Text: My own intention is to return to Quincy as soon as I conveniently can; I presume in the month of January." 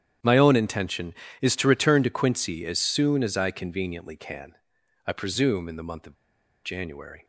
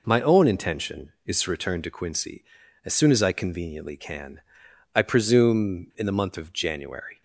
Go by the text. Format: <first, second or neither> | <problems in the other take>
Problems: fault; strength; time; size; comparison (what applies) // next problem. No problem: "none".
second | starts louder than the rest; strong; until 1.4 s; 10 dB // pauses between "of" and "January"; noticeable; at 6.1 s; 0.49 s long